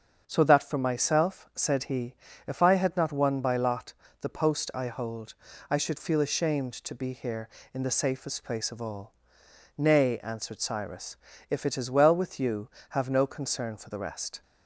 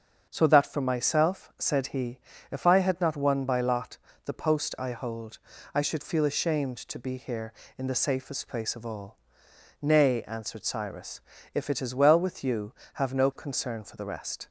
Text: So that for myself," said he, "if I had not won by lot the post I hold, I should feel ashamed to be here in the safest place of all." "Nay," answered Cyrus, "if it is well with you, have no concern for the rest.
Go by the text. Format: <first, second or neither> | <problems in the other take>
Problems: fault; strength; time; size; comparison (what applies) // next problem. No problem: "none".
neither | starts louder than the rest; the same in both // pauses between "lot" and "the"; slight; the same in both